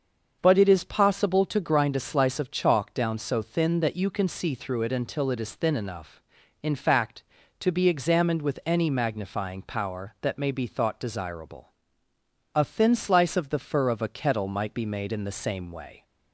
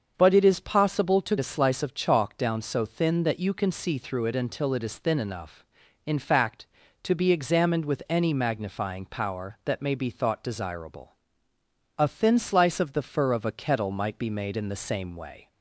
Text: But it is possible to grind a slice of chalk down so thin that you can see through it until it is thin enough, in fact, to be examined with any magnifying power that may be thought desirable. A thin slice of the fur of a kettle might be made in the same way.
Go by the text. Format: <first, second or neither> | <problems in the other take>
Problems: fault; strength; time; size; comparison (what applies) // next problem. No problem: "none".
first | starts louder than the rest; until 1.1 s; 7 dB; also in the first // skips "grind"; at 1.3 s